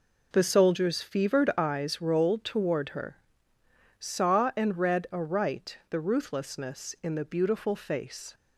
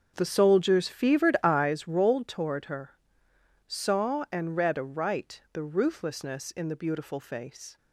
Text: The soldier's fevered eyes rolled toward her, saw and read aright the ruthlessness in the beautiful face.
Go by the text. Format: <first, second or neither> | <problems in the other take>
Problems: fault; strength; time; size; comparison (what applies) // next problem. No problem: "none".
first | starts louder than the rest; strong; until 1.8 s; 7 dB